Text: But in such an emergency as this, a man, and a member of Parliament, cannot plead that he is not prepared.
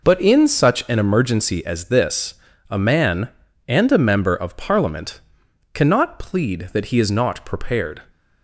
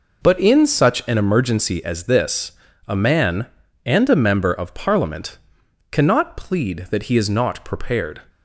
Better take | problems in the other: neither | none

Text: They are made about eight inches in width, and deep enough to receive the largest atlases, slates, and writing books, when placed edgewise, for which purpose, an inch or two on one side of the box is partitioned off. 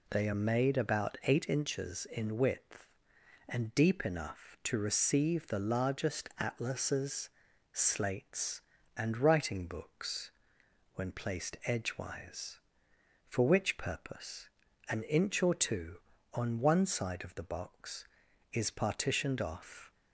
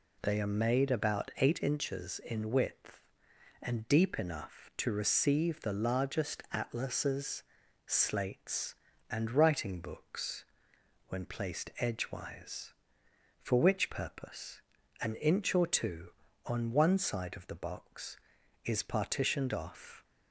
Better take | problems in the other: neither | none

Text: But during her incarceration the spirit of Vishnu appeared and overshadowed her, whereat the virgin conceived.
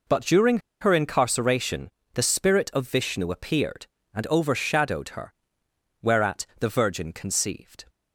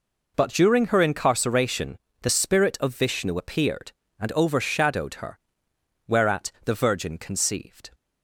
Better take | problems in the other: second | pauses between "during" and "her"; slight; at 0.5 s; 0.22 s long // pauses between "incarceration" and "the"; slight; at 1.8 s; 0.26 s long; slight in the second

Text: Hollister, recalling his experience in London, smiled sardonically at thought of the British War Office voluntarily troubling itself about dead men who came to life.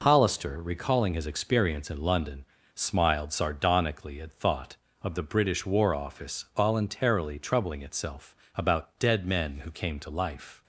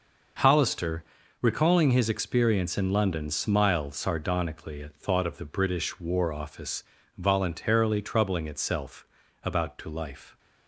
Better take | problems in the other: first | starts louder than the rest; noticeable; until 1.8 s; 6 dB // pauses between "Office" and "voluntarily"; slight; at 6.8 s; 0.34 s long // pauses between "itself" and "about"; slight; at 9.0 s; 0.36 s long; slight in the first // skips "dead men who came"; at 9.7 s

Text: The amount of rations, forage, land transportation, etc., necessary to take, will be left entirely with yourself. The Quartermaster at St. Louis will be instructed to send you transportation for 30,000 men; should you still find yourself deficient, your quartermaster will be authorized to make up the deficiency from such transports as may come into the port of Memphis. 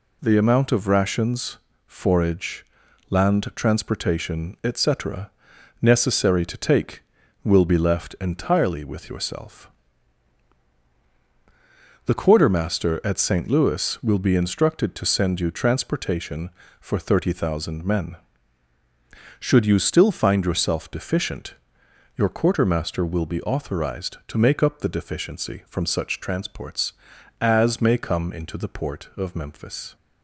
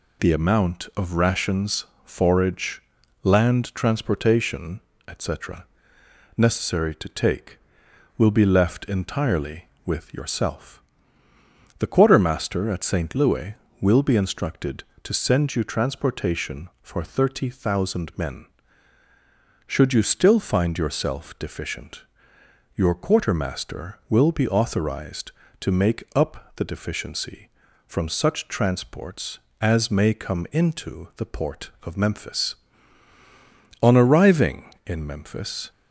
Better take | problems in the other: first | goes on to say "On arriving in Memphis"; strong; from 33.8 s on; 1.8 s long

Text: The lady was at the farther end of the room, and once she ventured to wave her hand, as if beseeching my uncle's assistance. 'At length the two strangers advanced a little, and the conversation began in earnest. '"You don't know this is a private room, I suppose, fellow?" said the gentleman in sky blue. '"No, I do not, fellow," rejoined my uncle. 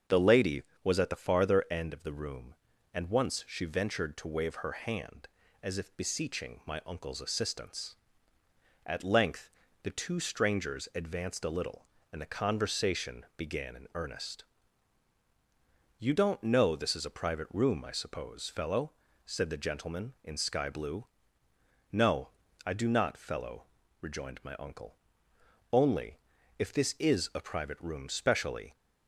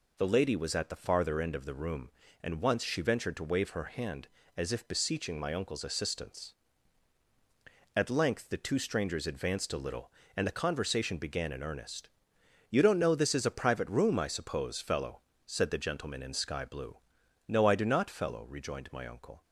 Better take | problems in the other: second | starts louder than the rest; until 1.2 s; 6.5 dB // pauses between "length" and "the"; slight; at 9.4 s; 0.34 s long // goes on to say "Only if this is a private room specially"; strong; from 25.7 s on; 3.0 s long

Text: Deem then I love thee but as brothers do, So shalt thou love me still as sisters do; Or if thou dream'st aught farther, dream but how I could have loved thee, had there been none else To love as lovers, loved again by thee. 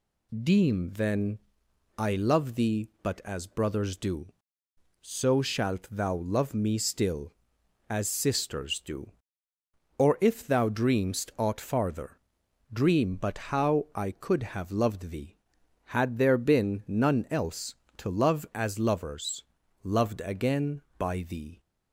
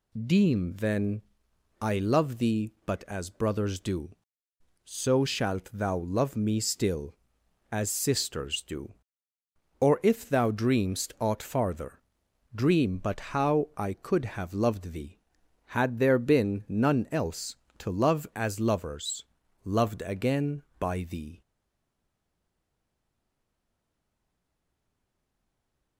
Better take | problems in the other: first | pauses between "then" and "I"; noticeable; at 1.2 s; 0.58 s long; noticeable in the first // stays silent after the last word; strong; from 21.4 s on; 4.5 s long

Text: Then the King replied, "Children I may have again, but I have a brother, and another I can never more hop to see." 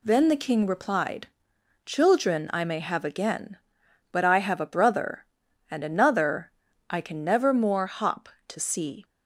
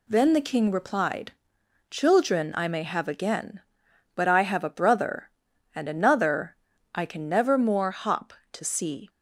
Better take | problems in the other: neither | pauses between "another" and "I"; the same in both

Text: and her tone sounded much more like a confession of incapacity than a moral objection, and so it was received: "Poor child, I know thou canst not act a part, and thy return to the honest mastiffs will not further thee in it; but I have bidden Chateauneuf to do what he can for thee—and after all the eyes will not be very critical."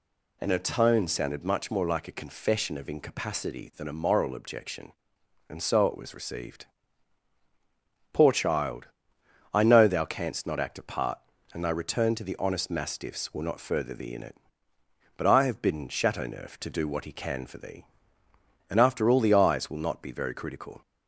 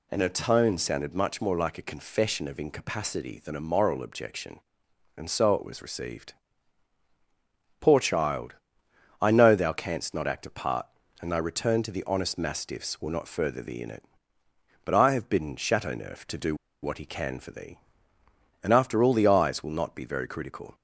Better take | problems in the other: first | pauses between "do" and "what"; slight; at 16.5 s; 0.27 s long

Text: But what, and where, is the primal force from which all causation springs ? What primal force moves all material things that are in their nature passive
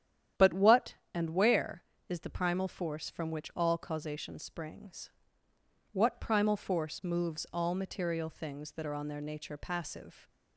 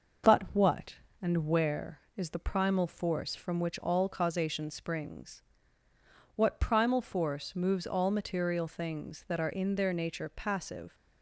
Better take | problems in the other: second | starts louder than the rest; strong; until 1.5 s; 10 dB; also in the second // says "on" for "in"; at 8.9 s

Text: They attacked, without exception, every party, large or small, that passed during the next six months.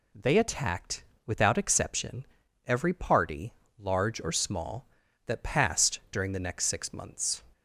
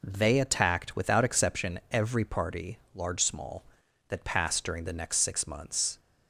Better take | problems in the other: first | skips "or"; at 3.2 s

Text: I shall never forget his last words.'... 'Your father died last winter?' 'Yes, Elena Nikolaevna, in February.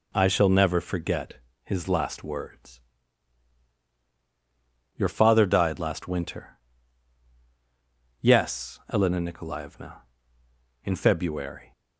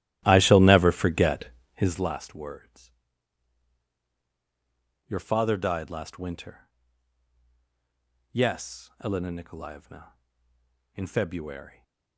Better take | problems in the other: first | starts louder than the rest; strong; until 2.1 s; 14 dB // pauses between "forget" and "his"; slight; at 1.4 s; 0.28 s long; slight in the first

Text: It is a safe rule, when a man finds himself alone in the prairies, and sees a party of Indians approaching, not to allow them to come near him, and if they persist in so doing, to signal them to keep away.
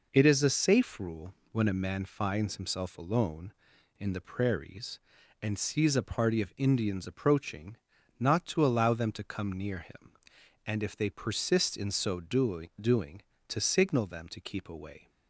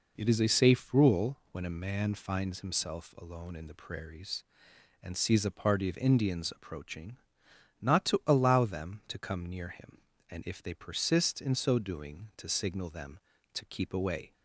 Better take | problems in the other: second | says "doing" twice; at 12.8 s

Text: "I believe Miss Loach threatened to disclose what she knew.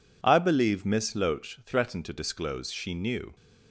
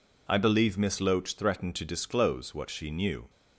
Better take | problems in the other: second | skips "what"; at 2.7 s

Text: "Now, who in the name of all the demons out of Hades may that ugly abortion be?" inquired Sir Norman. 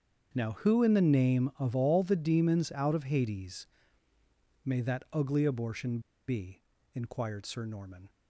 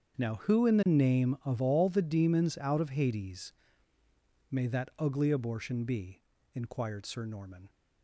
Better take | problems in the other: second | starts louder than the rest; strong; until 1.3 s; 7.5 dB; strong in the second // pauses between "Hades" and "may"; noticeable; at 3.6 s; 0.96 s long; noticeable in the second // pauses between "abortion" and "be"; slight; at 5.9 s; 0.28 s long

